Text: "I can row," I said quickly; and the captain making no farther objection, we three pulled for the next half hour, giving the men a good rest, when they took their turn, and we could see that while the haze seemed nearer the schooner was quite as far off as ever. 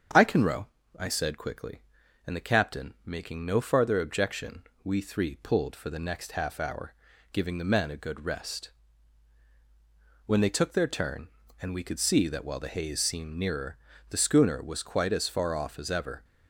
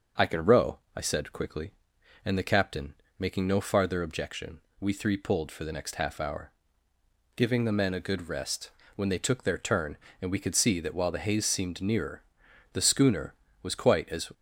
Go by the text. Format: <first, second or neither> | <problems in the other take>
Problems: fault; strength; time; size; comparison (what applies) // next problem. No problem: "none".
first | starts louder than the rest; until 1.3 s; 6 dB; strong in the first // pauses between "captain" and "making"; slight; at 2.9 s; 0.26 s long // pauses between "nearer" and "the"; noticeable; at 12.2 s; 0.52 s long; slight in the first // stops before "far off as ever"; at 14.3 s